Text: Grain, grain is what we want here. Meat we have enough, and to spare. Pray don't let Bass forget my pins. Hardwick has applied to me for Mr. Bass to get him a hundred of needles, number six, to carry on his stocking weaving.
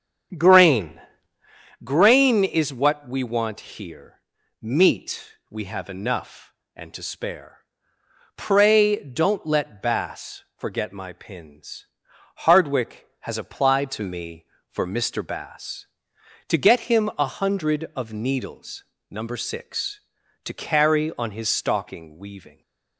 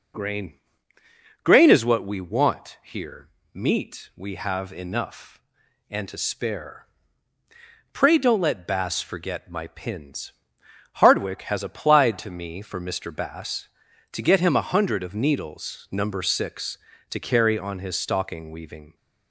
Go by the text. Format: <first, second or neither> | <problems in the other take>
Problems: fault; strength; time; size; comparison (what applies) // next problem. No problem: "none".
second | starts louder than the rest; strong; until 1.6 s; 8 dB // pauses between "want" and "here"; slight; at 3.5 s; 0.16 s long